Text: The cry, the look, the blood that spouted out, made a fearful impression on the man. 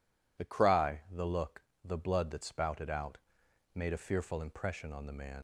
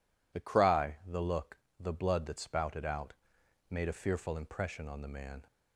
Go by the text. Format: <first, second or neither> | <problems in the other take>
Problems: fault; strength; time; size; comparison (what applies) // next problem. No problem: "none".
second | leaves "man" unfinished; at 5.3 s; 90 ms